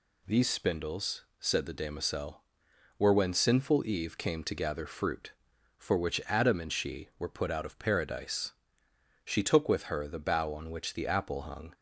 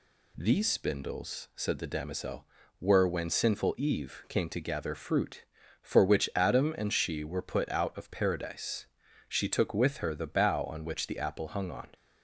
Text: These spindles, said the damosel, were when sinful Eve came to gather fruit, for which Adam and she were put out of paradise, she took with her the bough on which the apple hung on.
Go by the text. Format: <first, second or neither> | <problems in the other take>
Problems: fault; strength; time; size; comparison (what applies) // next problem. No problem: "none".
second | stops before "on"; at 11.7 s